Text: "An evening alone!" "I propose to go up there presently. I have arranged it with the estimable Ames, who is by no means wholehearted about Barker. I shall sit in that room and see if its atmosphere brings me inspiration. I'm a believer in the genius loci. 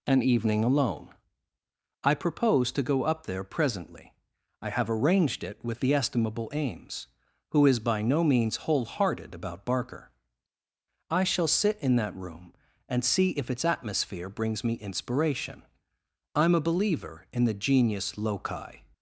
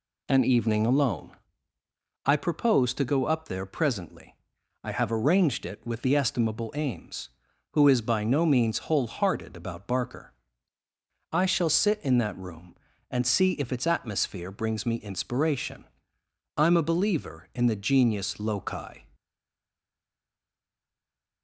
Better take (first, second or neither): first